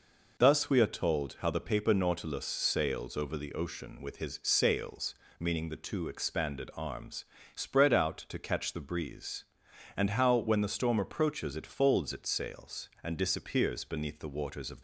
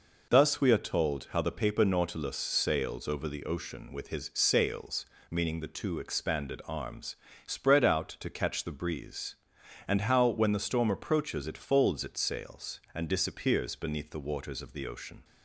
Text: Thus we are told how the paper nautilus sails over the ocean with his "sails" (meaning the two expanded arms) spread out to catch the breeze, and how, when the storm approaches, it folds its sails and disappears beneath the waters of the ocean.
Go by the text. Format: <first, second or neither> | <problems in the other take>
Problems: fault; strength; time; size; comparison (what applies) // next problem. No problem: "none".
second | stops before "the ocean"; at 14.7 s